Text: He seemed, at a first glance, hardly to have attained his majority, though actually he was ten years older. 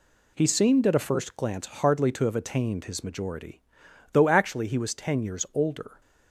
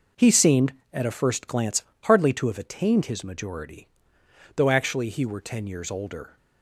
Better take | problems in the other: first | says "were" for "was"; at 5.2 s

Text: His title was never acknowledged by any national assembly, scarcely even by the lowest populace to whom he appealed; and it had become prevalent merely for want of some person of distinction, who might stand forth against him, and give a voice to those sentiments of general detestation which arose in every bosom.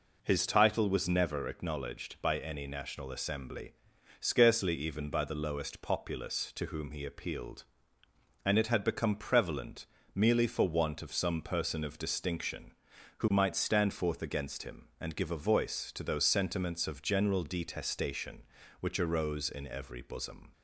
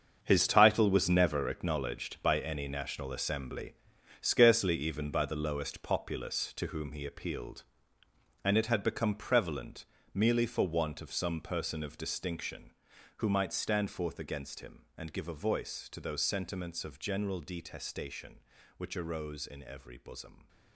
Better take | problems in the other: first | gets quieter; strong; throughout; 12 dB // pauses between "prevalent" and "merely"; slight; at 9.8 s; 0.28 s long; slight in the first

